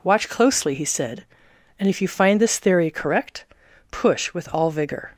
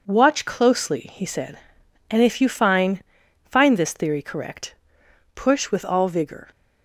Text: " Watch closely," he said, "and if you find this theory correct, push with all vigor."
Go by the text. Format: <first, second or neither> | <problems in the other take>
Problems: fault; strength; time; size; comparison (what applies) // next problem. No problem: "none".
first | says "find" twice; at 3.4 s